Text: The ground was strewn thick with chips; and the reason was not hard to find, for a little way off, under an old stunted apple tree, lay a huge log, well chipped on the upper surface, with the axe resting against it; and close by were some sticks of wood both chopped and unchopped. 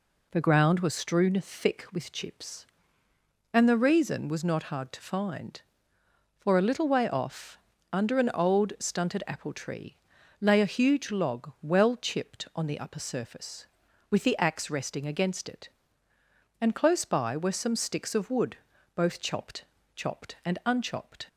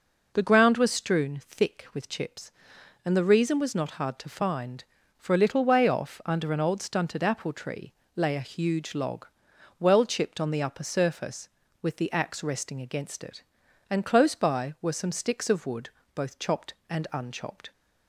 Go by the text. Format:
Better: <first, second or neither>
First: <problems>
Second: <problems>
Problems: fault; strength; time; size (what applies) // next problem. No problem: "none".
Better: second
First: pauses between "wood" and "both"; slight; at 18.5 s; 0.36 s long // says "chopped" twice; at 19.9 s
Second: pauses between "wood" and "both"; slight; at 15.8 s; 0.26 s long